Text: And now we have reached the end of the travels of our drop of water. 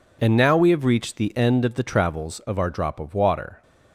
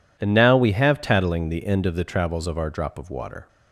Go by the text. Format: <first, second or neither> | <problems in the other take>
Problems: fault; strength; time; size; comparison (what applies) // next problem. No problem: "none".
first | says "tattling" for "reached"; at 1.0 s